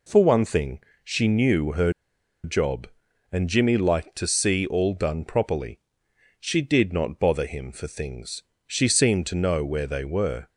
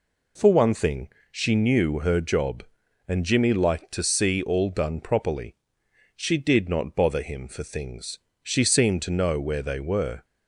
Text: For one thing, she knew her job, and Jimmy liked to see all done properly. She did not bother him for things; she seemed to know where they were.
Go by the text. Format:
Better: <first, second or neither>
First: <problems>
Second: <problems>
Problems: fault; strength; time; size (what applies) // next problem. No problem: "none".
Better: second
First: pauses between "her" and "job"; noticeable; at 1.9 s; 0.52 s long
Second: none